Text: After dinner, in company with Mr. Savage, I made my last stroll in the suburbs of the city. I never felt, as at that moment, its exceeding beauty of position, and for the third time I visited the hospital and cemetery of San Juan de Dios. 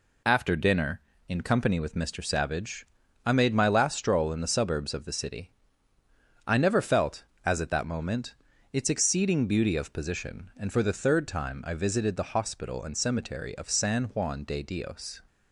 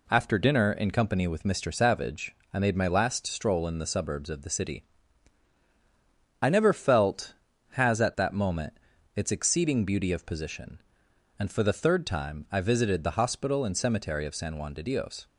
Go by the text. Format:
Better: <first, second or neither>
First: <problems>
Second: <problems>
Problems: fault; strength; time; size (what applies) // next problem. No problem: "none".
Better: first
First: none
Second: says "has" for "as"; at 7.7 s